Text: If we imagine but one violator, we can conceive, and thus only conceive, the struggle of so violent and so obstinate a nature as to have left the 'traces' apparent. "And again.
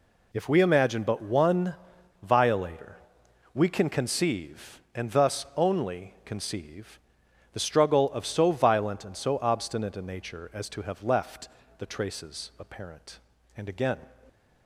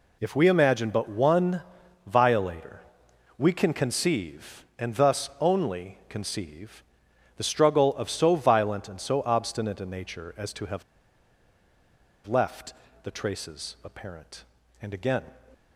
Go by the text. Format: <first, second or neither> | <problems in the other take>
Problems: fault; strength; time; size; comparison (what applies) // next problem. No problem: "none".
first | pauses between "one" and "violator"; at 1.6 s; 0.44 s long; noticeable in the first // pauses between "have" and "left"; strong; at 10.8 s; 1.4 s long // pauses between "left" and "the"; slight; at 12.7 s; 0.30 s long; slight in the first